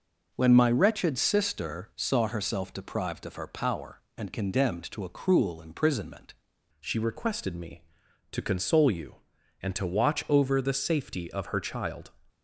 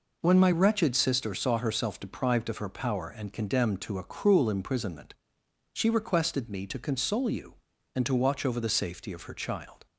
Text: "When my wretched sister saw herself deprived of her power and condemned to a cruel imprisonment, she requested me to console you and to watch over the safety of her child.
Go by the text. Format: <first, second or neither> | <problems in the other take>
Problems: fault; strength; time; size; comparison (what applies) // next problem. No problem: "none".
second | changes voice at "she"; from 6.8 s on; 5.3 s long